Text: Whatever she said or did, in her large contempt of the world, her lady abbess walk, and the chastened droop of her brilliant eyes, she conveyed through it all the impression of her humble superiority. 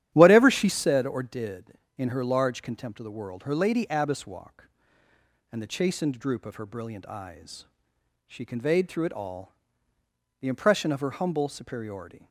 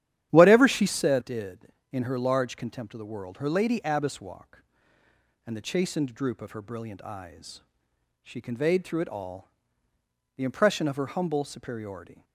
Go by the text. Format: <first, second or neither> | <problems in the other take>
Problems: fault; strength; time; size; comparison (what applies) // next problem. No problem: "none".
first | starts louder than the rest; strong; until 1.3 s; 11 dB; strong in the first // skips "or"; at 1.2 s // pauses between "all" and "the"; noticeable; at 9.4 s; 0.86 s long; noticeable in the first